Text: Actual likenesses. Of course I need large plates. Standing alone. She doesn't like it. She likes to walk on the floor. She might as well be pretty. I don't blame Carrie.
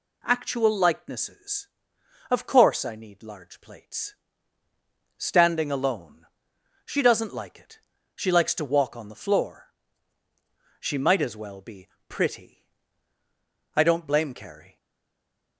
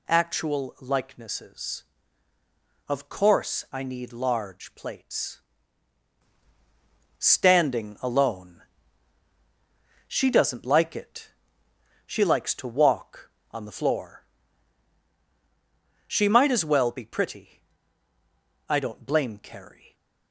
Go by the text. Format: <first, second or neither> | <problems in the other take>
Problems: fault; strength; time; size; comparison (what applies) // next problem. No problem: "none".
second | pauses between "be" and "pretty"; slight; at 11.8 s; 0.20 s long // stays silent after the last word; slight; from 14.7 s on; 0.8 s long